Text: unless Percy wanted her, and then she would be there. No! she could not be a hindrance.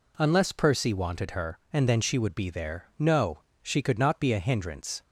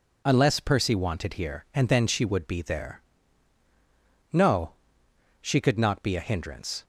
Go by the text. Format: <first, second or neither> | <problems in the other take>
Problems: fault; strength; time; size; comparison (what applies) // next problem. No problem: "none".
first | says "here" for "her"; at 1.3 s